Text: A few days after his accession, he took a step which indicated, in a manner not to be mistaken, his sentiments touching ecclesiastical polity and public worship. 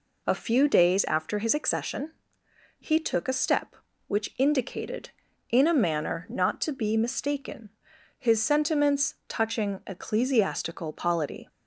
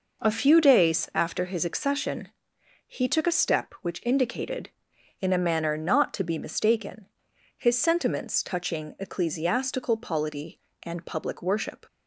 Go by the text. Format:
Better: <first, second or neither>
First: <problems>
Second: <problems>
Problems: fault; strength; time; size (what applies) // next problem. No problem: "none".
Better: second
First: stops before "and public worship"; at 11.4 s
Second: none